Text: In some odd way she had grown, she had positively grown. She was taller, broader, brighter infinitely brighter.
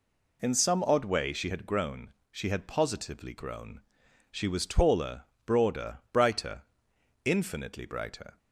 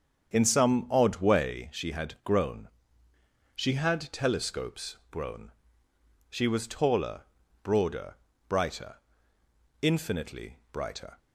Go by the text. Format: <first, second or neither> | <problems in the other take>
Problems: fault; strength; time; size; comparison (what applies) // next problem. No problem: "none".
first | starts louder than the rest; strong; until 1.3 s; 7.5 dB // says "telescopes" for "positively"; at 4.1 s // pauses between "brighter" and "infinitely"; noticeable; at 8.9 s; 0.86 s long; noticeable in the first // pauses between "infinitely" and "brighter"; slight; at 10.5 s; 0.16 s long